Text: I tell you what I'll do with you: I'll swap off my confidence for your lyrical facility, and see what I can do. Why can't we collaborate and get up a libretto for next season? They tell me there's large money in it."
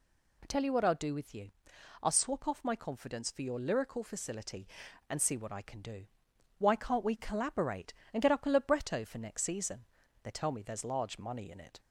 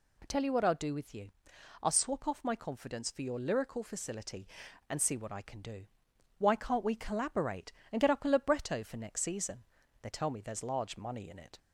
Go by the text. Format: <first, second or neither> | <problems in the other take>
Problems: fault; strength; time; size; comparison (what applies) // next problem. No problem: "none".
neither | none